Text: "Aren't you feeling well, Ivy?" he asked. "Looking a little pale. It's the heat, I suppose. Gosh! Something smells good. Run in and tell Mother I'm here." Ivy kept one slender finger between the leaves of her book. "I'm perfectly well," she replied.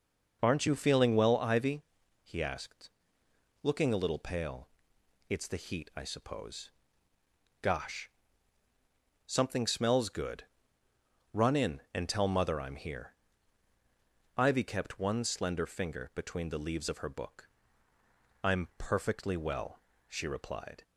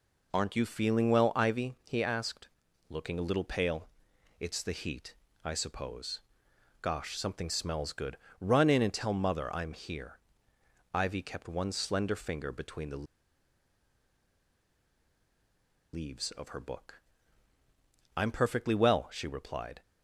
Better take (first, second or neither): first